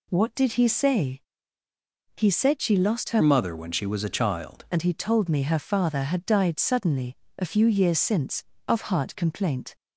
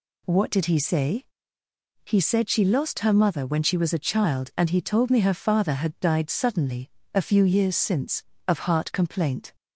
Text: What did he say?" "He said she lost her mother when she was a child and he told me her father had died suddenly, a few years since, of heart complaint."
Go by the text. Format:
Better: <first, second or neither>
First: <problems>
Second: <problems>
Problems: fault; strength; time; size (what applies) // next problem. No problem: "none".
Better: second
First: changes voice from "mother" to "child"; from 3.2 to 4.6 s; 1.4 s long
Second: none